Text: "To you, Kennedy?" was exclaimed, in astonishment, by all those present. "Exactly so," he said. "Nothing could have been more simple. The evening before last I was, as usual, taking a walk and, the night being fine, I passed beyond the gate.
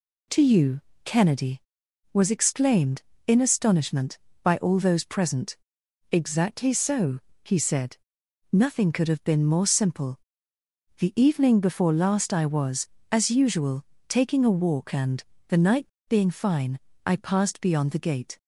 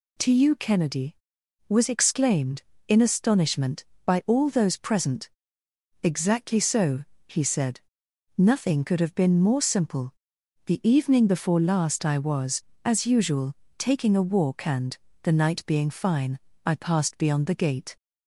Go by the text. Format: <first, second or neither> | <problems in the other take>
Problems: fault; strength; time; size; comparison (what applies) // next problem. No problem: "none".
second | pauses between "night" and "being"; slight; at 15.8 s; 0.19 s long